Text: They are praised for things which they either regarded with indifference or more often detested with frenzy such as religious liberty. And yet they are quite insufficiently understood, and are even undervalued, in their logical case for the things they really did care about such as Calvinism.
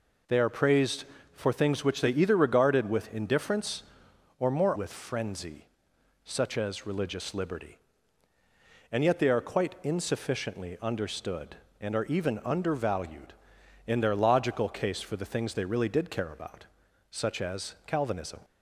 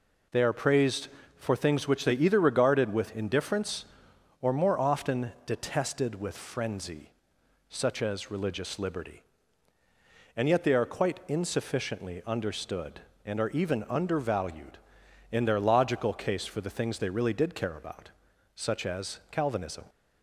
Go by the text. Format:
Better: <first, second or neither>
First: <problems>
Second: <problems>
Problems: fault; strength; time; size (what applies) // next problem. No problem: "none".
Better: second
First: skips "often detested"; at 4.7 s // pauses between "frenzy" and "such"; noticeable; at 5.6 s; 0.58 s long // pauses between "about" and "such"; at 16.6 s; 0.44 s long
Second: pauses between "frenzy" and "such"; noticeable; at 7.1 s; 0.58 s long // pauses between "about" and "such"; at 18.1 s; 0.44 s long